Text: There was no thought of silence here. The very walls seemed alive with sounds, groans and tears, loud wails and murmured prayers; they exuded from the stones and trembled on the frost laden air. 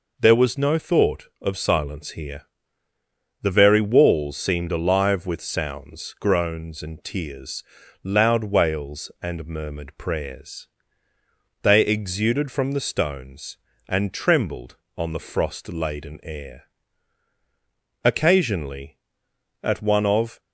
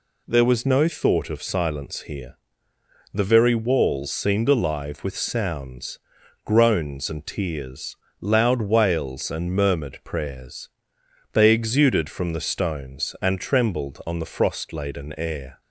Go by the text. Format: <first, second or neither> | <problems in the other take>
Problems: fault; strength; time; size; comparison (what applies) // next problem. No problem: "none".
second | goes on to say "Occasionally at one of"; strong; from 18.0 s on; 2.3 s long